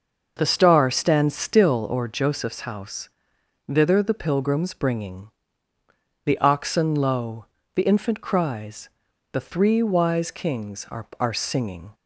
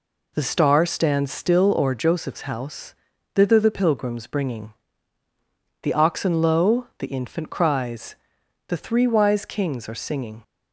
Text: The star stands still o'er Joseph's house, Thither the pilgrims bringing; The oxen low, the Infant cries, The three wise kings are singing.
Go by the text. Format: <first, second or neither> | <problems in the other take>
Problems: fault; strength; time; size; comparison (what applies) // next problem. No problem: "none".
second | starts louder than the rest; noticeable; until 1.3 s; 6 dB // says "are" twice; at 11.1 s